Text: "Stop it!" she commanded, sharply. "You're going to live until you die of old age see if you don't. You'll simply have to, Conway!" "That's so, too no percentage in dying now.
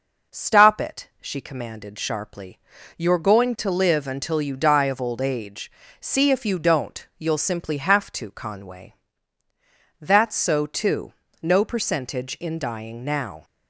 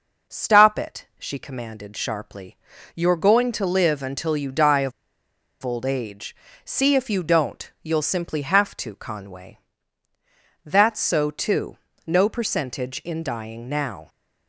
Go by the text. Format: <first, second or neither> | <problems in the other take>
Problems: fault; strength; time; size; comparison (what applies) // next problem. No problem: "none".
first | pauses between "of" and "old"; noticeable; at 4.9 s; 0.70 s long // pauses between "age" and "see"; slight; at 6.3 s; 0.30 s long; slight in the first // pauses between "too" and "no"; slight; at 11.7 s; 0.30 s long; slight in the first